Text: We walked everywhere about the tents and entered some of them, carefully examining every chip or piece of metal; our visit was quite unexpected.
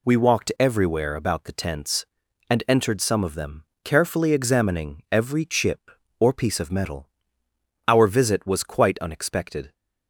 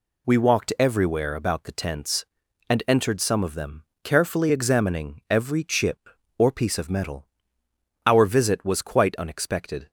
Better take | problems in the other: neither | none

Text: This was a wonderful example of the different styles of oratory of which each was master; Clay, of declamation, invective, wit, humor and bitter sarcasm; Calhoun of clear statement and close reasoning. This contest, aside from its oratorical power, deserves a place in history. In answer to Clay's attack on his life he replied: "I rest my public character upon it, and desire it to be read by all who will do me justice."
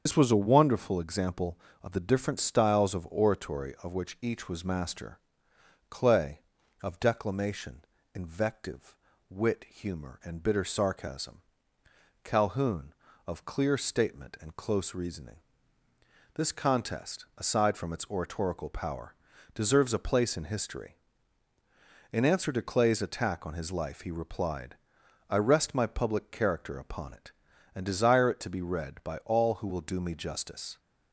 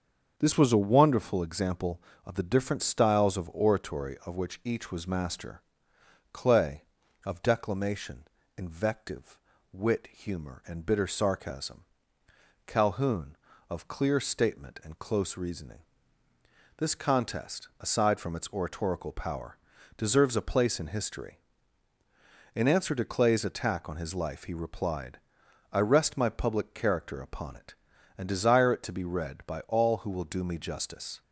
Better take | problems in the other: second | loses the start of "This"; at 0.0 s; 85 ms // starts louder than the rest; strong; until 1.0 s; 7.5 dB; strong in the second

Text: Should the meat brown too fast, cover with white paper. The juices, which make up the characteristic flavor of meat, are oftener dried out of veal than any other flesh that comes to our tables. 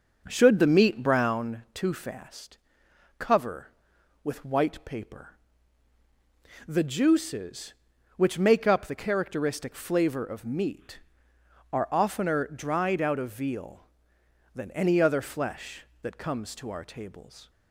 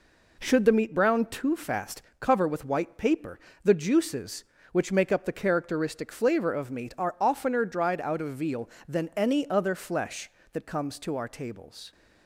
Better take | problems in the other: second | starts louder than the rest; noticeable; until 1.5 s; 6 dB

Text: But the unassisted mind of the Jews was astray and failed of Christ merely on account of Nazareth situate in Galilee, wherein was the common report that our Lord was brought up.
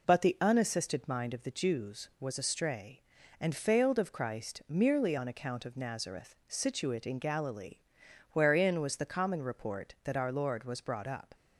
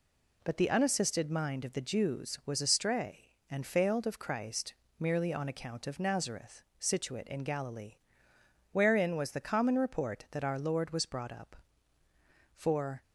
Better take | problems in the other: first | pauses between "Christ" and "merely"; slight; at 4.7 s; 0.24 s long // pauses between "Nazareth" and "situate"; slight; at 6.6 s; 0.16 s long // goes on to say "For"; slight; from 12.5 s on; 0.48 s long

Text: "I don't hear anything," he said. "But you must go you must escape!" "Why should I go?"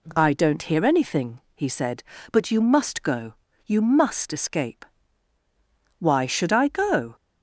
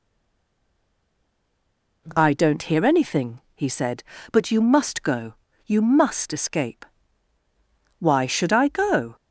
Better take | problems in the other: first | stays silent before the first word; noticeable; until 2.0 s; 2.0 s long // pauses between "go" and "you"; slight; at 5.3 s; 0.30 s long; slight in the first

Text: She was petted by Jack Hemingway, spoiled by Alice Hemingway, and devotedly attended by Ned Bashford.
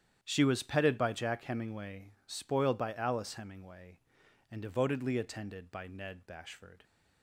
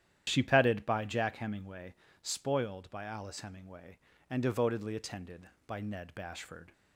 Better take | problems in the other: first | starts louder than the rest; strong; until 1.2 s; 11 dB; strong in the first // skips "was"; at 0.4 s

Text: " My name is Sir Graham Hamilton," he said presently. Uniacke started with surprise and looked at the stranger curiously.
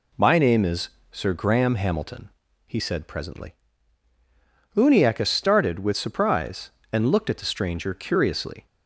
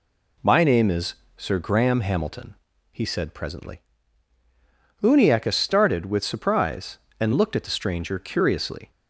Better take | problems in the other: neither | pauses between "is" and "Sir"; slight; the same in both

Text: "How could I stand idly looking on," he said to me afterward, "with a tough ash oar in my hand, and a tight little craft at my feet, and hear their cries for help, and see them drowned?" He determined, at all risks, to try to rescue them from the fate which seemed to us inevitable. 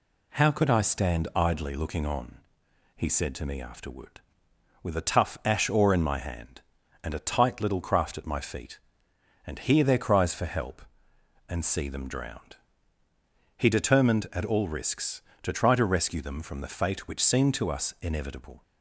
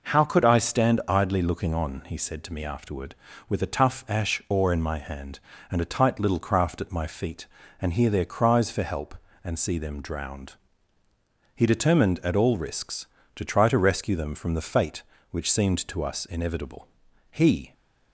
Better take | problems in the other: first | goes on to say "He"; slight; from 17.3 s on; 0.42 s long

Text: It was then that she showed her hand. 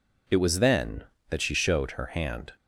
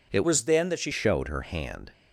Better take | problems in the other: first | changes voice from "was" to "she"; from 0.2 to 0.9 s; 0.7 s long

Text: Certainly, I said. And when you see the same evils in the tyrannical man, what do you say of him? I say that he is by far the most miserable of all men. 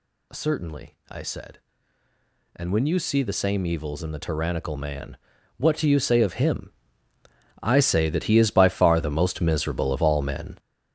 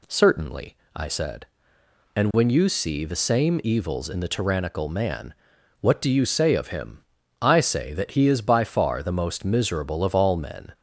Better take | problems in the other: second | gets louder; strong; throughout; 9.5 dB

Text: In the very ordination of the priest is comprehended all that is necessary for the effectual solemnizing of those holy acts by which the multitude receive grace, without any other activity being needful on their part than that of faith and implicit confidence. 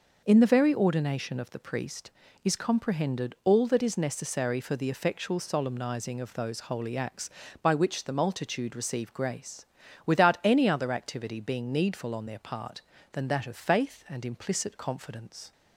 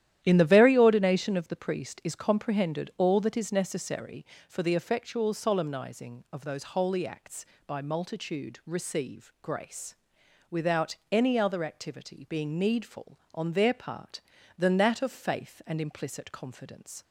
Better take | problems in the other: first | starts louder than the rest; strong; until 1.2 s; 12 dB // skips "which the"; at 7.8 s // pauses between "without" and "any"; slight; at 10.9 s; 0.16 s long

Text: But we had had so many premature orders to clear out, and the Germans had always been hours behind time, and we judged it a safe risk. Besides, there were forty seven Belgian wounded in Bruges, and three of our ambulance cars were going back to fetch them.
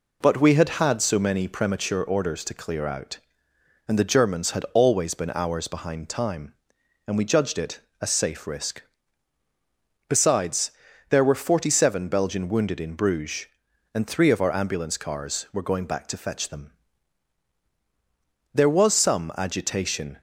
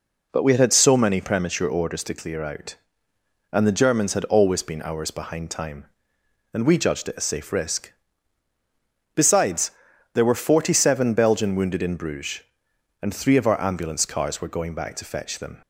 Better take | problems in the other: second | pauses between "it" and "a"; slight; at 7.8 s; 0.20 s long // goes on to say "There was some agitation"; strong; from 18.5 s on; 1.6 s long

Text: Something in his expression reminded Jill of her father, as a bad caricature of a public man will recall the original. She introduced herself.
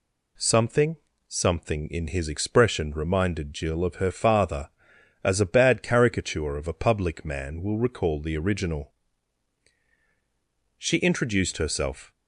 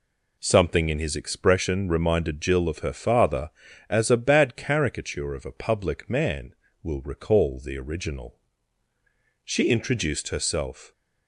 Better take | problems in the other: second | says "Something" twice; at 1.2 s

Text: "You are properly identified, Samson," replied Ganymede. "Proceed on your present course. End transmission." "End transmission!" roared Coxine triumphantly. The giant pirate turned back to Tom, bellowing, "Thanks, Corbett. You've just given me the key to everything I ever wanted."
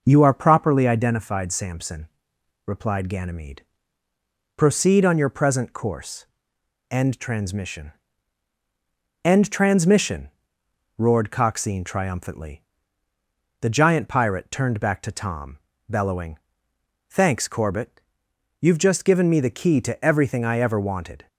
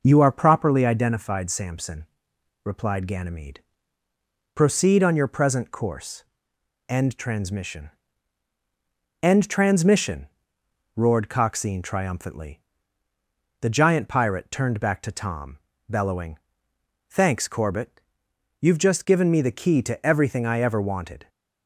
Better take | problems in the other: neither | none

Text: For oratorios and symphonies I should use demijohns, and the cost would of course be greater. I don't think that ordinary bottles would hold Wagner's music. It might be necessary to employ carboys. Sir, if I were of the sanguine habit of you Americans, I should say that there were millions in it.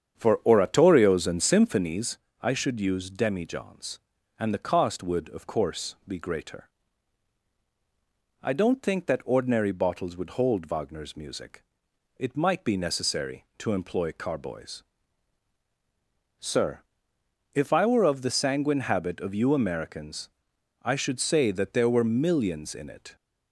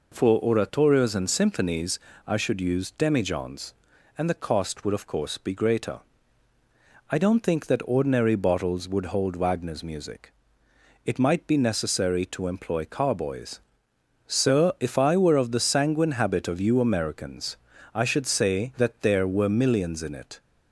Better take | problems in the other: second | starts louder than the rest; strong; until 2.0 s; 8 dB // pauses between "symphonies" and "I"; slight; at 2.1 s; 0.24 s long; slight in the second

